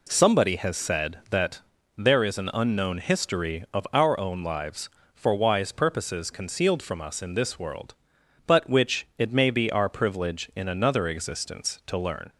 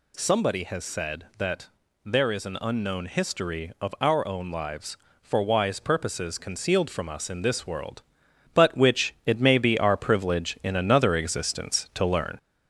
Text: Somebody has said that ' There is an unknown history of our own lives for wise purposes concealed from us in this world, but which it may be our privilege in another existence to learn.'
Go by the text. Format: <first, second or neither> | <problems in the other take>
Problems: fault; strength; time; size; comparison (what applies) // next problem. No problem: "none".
first | gets louder; noticeable; throughout; 5 dB